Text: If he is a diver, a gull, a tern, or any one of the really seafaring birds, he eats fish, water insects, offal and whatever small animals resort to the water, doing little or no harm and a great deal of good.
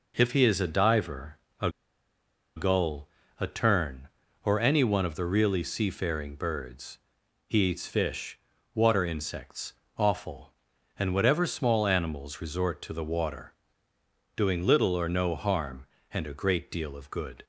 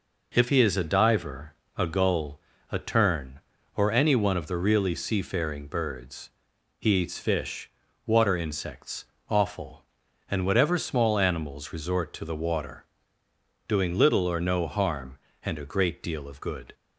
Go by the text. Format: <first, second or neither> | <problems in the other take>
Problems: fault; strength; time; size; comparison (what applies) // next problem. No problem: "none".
second | pauses between "a" and "gull"; noticeable; at 1.6 s; 0.87 s long